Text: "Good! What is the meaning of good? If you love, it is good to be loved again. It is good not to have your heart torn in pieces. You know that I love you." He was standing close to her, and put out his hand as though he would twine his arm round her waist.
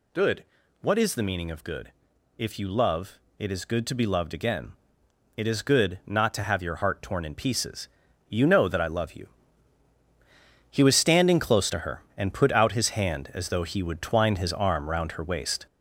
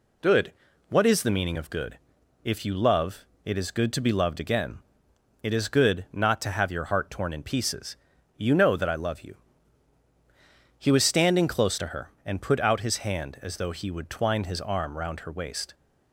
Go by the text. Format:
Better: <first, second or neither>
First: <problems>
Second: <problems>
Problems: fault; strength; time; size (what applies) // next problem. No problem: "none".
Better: second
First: gets louder; noticeable; throughout; 5 dB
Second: none